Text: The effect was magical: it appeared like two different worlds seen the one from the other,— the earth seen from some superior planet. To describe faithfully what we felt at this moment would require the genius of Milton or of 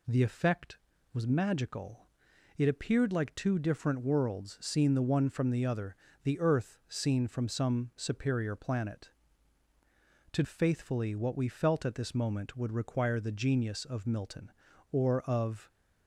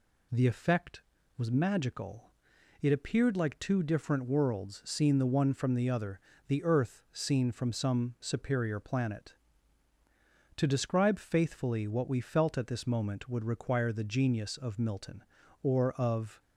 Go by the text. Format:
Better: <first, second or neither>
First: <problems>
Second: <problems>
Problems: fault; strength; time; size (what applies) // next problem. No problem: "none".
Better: second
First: skips "describe"; at 10.4 s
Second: none